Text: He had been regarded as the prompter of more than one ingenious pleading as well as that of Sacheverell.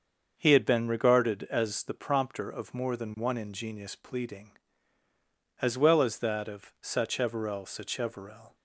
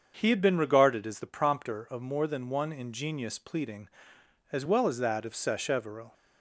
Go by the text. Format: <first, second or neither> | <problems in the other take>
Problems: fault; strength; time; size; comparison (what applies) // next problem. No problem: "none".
second | starts louder than the rest; until 1.3 s; 6.5 dB; also in the second // says "Sacheverell" twice; at 7.6 s